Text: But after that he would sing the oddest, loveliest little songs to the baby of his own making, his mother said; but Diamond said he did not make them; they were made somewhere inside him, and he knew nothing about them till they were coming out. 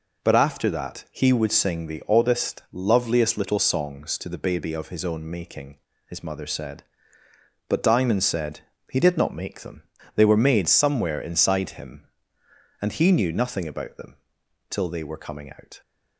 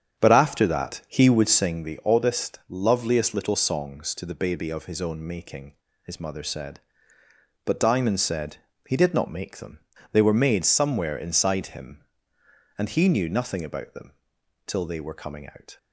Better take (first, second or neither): first